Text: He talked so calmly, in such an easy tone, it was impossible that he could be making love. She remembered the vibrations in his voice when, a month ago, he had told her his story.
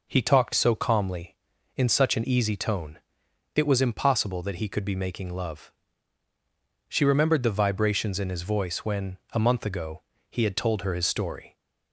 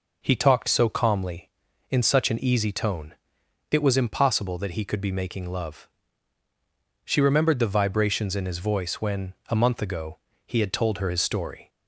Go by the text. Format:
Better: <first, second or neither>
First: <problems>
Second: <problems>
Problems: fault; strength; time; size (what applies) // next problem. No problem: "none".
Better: neither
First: none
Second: none